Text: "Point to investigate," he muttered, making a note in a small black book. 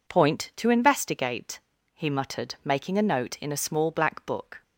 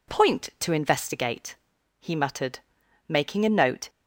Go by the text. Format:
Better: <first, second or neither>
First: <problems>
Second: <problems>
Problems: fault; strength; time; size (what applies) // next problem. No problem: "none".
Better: first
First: none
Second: stops before "in a small black book"; at 3.8 s